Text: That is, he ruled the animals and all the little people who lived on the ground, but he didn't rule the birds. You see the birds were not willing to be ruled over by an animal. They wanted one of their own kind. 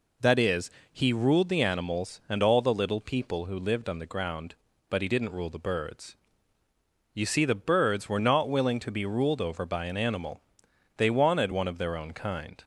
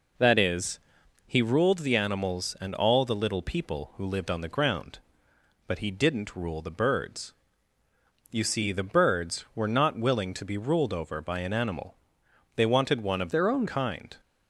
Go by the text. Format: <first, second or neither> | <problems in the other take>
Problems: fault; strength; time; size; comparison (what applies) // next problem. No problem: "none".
first | changes voice from "their" to "own"; from 13.3 to 13.6 s; 0.3 s long